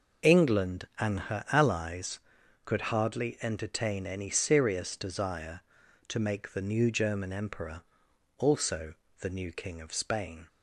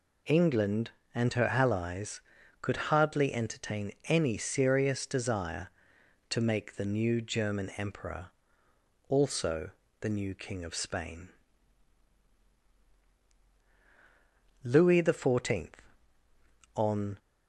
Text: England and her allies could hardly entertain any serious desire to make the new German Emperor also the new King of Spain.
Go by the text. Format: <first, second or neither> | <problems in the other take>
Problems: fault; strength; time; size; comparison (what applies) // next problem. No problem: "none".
first | pauses between "Emperor" and "also"; noticeable; at 8.2 s; 0.78 s long; noticeable in the first // pauses between "also" and "the"; slight; at 9.6 s; 0.30 s long; slight in the first // goes on to say "Louis the Fourteenth on"; strong; from 14.6 s on; 2.5 s long